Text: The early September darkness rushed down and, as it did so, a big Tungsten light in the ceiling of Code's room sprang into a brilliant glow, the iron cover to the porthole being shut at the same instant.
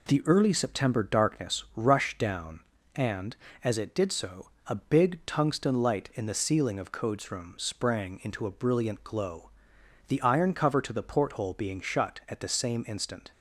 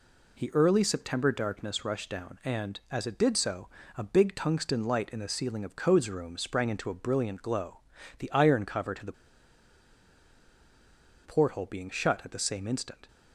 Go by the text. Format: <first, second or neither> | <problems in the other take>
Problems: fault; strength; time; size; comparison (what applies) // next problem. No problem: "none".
first | pauses between "the" and "porthole"; strong; at 9.1 s; 2.1 s long